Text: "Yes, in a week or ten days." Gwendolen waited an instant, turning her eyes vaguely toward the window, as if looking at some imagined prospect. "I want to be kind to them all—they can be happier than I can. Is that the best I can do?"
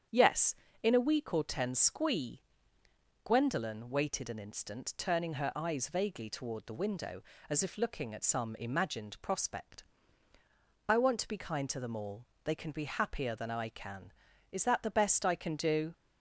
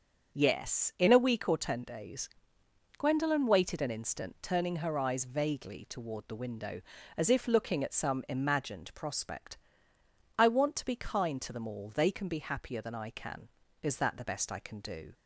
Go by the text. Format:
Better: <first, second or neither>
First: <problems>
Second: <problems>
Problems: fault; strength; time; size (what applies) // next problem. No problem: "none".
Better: second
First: starts louder than the rest; strong; until 1.3 s; 8 dB // says "squee" for "days"; at 1.7 s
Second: starts louder than the rest; until 1.4 s; 6.5 dB